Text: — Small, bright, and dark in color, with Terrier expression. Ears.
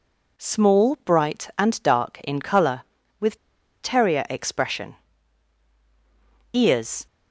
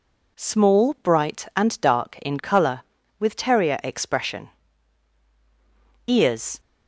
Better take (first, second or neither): second